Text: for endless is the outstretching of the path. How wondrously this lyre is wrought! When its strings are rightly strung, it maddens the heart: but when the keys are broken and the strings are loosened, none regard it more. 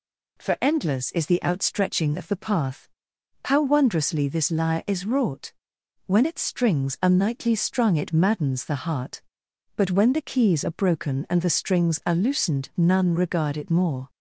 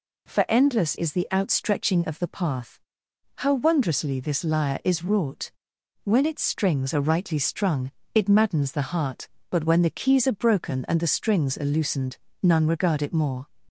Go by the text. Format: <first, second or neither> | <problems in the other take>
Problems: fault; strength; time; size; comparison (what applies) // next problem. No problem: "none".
second | says "nightly" for "rightly"; at 7.0 s